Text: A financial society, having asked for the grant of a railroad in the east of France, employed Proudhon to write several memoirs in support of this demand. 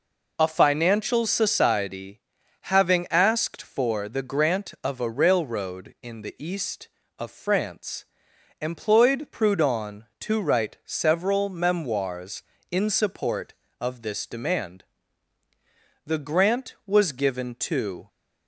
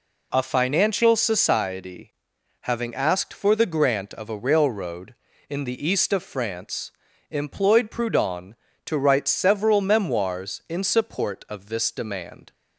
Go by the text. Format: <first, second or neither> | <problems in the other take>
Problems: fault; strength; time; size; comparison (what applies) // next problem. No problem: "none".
second | goes on to say "The grant was given to"; strong; from 16.0 s on; 2.0 s long